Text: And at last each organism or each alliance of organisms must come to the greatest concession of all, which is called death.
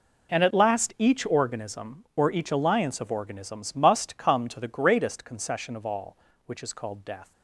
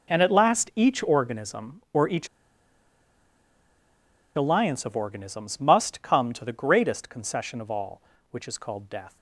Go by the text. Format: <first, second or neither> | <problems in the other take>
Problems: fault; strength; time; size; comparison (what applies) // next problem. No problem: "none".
first | pauses between "each" and "alliance"; strong; at 2.2 s; 2.0 s long